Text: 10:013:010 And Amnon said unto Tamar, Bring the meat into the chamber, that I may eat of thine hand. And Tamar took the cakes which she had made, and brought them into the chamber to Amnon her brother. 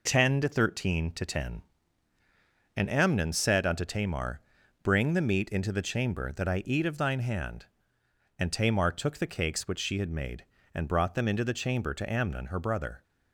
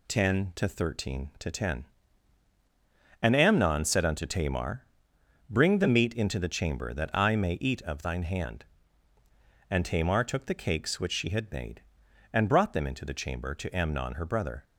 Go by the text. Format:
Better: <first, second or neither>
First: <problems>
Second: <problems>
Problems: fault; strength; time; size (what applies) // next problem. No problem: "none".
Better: second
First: skips "may"; at 6.6 s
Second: none